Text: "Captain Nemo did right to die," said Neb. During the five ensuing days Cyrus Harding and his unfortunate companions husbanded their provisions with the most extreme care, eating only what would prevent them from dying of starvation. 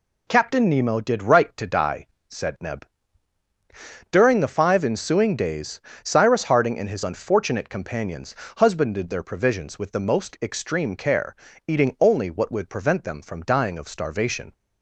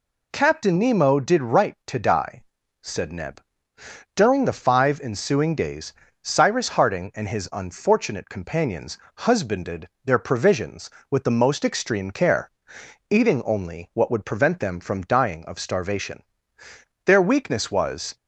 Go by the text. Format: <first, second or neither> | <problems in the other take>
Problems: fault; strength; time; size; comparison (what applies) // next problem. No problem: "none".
first | pauses between "days" and "Cyrus"; slight; at 5.9 s; 0.28 s long; slight in the first // pauses between "companions" and "husbanded"; slight; at 8.9 s; 0.18 s long; slight in the first // pauses between "husbanded" and "their"; slight; at 9.8 s; 0.16 s long // goes on to say "Their weakness was"; noticeable; from 17.0 s on; 1.1 s long